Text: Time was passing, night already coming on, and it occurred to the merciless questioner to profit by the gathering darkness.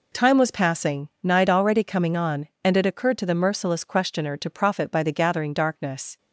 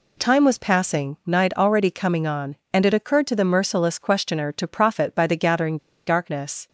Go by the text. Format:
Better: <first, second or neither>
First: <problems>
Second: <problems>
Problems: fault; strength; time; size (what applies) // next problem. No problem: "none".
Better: first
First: none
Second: pauses between "gathering" and "darkness"; slight; at 5.7 s; 0.30 s long